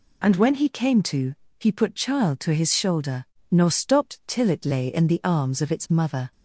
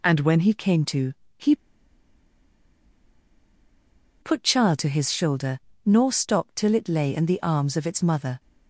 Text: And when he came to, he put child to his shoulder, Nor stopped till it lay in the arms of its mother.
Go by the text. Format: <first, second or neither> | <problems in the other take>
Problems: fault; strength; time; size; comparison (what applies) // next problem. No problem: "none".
first | pauses between "he" and "put"; strong; at 1.5 s; 2.6 s long